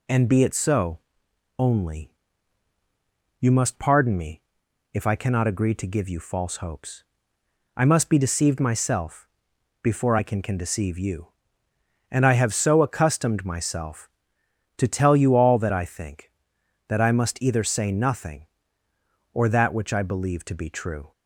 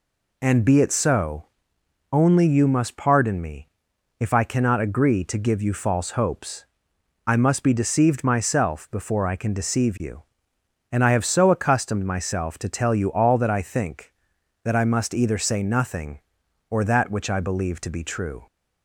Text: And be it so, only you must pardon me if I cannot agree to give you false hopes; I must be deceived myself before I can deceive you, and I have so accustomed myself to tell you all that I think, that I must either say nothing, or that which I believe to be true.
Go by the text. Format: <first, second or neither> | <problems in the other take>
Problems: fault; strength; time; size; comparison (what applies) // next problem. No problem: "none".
second | pauses between "only" and "you"; strong; at 2.0 s; 1.3 s long // pauses between "me" and "if"; noticeable; at 4.4 s; 0.52 s long; noticeable in the second // pauses between "myself" and "before"; noticeable; at 9.2 s; 0.52 s long // says "can" twice; at 10.4 s